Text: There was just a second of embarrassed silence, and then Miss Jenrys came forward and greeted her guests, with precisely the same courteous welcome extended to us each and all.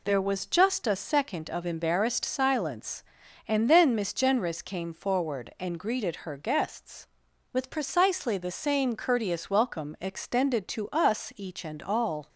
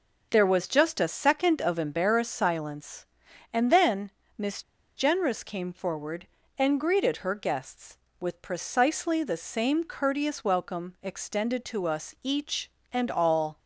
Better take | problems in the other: first | pauses between "then" and "Miss"; slight; at 4.1 s; 0.26 s long // pauses between "Miss" and "Jenrys"; slight; at 4.6 s; 0.36 s long

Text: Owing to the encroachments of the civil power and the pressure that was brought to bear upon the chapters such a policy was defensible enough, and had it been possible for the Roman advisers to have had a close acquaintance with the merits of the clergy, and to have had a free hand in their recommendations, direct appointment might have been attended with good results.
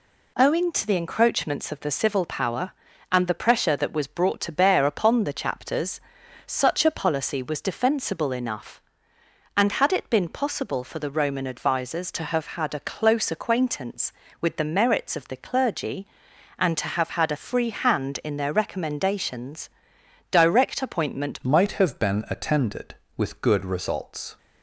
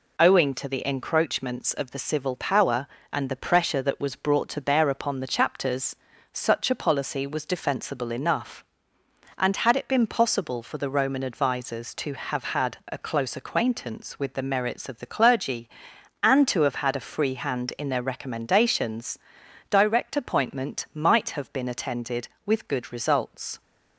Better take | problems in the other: second | pauses between "chapters" and "such"; noticeable; at 5.9 s; 0.48 s long; slight in the second // changes voice at "might"; from 21.4 s on; 2.9 s long

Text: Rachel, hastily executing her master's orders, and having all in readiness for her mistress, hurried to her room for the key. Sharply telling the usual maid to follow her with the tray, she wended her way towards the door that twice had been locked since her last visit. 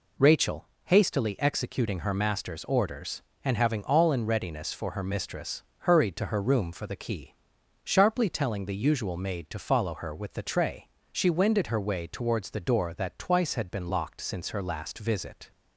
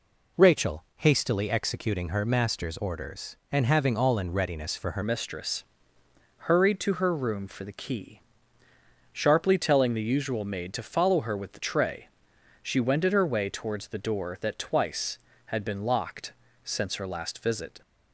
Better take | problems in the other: first | changes voice at "mistress"; from 5.0 s on; 12.8 s long // pauses between "locked" and "since"; slight; at 16.3 s; 0.32 s long

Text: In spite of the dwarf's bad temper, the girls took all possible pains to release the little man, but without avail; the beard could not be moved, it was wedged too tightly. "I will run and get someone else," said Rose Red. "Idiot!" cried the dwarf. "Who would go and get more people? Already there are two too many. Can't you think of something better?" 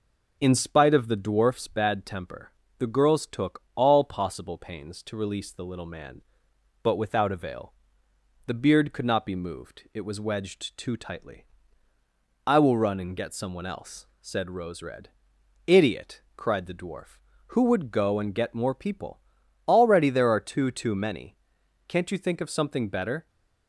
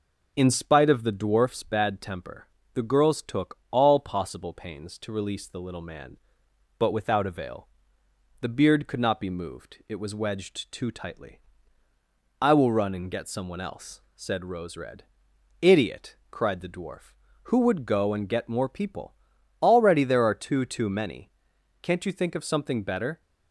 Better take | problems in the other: neither | none

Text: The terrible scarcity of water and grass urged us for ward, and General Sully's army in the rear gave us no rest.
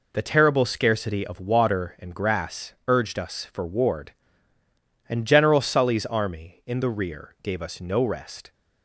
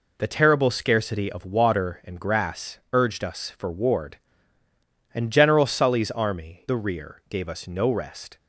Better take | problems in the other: first | skips "in"; at 6.6 s

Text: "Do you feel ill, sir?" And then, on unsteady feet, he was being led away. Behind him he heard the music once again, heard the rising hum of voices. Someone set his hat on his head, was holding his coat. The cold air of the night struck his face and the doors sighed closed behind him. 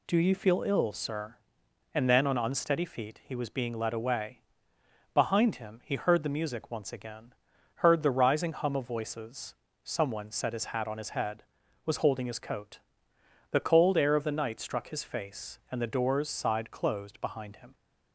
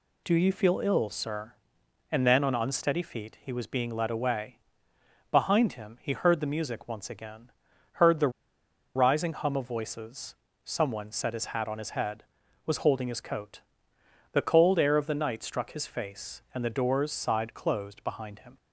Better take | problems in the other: first | pauses between "the" and "rising"; noticeable; at 8.2 s; 0.66 s long

